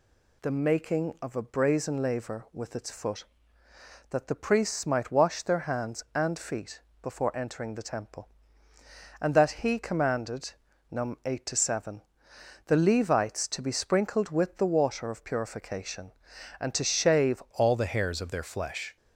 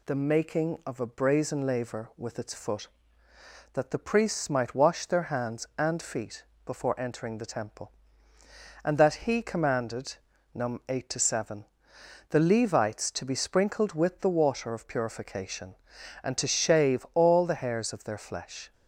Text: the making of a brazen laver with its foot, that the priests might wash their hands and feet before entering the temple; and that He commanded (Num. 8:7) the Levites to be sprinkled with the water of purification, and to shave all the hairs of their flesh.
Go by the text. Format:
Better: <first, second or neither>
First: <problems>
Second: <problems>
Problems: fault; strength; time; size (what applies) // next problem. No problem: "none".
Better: second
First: pauses between "feet" and "before"; slight; at 6.8 s; 0.22 s long // changes voice at "all"; from 17.5 s on; 1.4 s long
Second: pauses between "feet" and "before"; slight; at 6.4 s; 0.22 s long